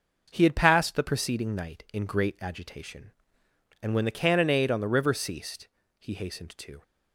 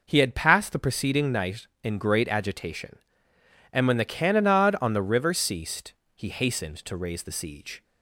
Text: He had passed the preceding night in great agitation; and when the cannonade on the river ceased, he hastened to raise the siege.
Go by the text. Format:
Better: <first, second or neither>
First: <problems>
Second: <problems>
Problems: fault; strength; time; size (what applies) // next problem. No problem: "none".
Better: second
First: stops before "raise the siege"; at 6.8 s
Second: none